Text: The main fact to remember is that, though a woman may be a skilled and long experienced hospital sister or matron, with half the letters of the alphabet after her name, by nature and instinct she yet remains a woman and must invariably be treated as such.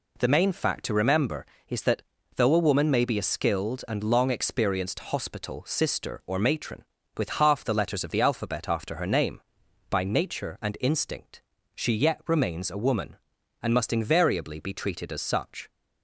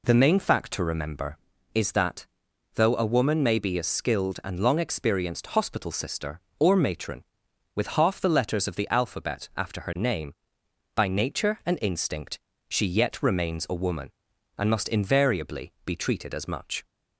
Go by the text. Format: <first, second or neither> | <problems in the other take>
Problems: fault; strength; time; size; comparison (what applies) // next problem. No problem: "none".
first | pauses between "instinct" and "she"; slight; at 12.3 s; 0.30 s long; slight in the first // says "much" for "such"; at 16.4 s